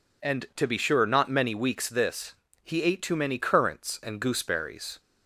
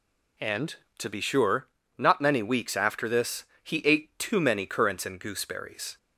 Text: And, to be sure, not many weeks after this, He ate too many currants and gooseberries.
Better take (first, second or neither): second